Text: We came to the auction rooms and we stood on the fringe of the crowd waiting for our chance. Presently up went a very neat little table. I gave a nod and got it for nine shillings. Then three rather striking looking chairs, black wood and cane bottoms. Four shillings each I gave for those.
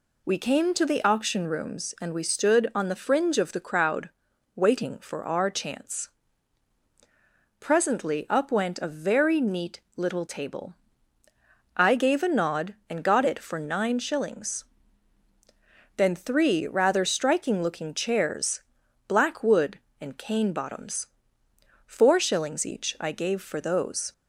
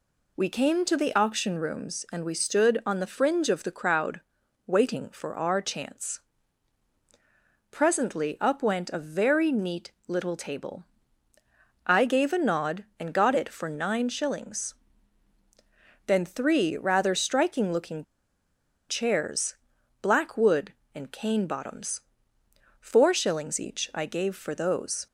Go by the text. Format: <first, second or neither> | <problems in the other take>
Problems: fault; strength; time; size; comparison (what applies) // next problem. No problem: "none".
first | pauses between "crowd" and "waiting"; noticeable; at 4.2 s; 0.46 s long; noticeable in the first // pauses between "looking" and "chairs"; noticeable; at 18.0 s; 0.86 s long